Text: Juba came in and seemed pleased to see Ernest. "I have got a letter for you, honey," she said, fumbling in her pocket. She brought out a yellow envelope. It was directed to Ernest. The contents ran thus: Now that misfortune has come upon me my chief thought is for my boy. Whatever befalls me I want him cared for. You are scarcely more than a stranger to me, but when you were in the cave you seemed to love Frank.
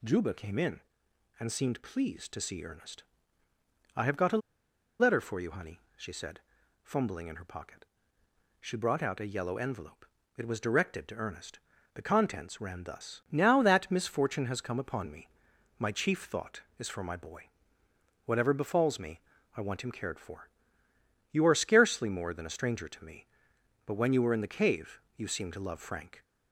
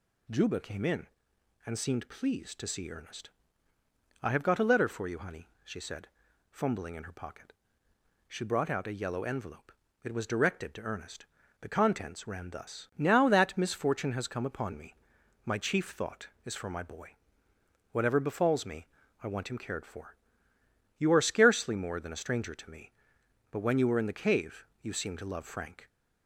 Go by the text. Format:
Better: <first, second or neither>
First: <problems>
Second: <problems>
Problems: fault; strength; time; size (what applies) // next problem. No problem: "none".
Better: second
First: pauses between "a" and "letter"; noticeable; at 4.3 s; 0.61 s long // pauses between "me" and "my"; noticeable; at 15.2 s; 0.48 s long // pauses between "me" and "I"; slight; at 19.1 s; 0.36 s long // pauses between "cave" and "you"; slight; at 24.9 s; 0.18 s long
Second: pauses between "me" and "my"; noticeable; at 14.9 s; 0.48 s long // pauses between "me" and "I"; slight; at 18.8 s; 0.36 s long // pauses between "cave" and "you"; slight; at 24.6 s; 0.18 s long